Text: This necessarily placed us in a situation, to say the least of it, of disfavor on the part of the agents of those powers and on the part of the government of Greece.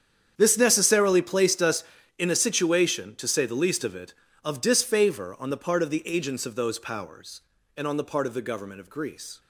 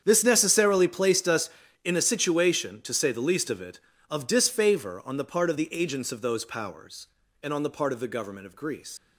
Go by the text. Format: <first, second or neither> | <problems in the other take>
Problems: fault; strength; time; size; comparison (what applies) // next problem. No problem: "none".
first | starts louder than the rest; strong; until 1.0 s; 8 dB; strong in the first // leaves "Greece" unfinished; at 8.9 s; 90 ms